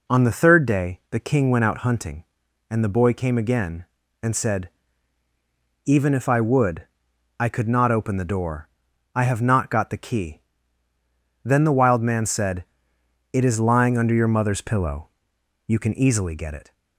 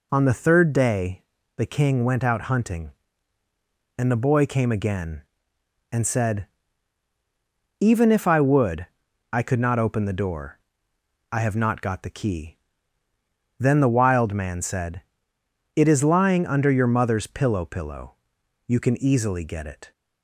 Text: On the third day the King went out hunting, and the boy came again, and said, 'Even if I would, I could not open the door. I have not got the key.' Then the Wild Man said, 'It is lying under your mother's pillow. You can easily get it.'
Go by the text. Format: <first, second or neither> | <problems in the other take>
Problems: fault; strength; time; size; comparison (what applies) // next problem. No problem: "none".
first | pauses between "day" and "the"; slight; at 1.2 s; 0.34 s long // says "pillow" twice; at 17.6 s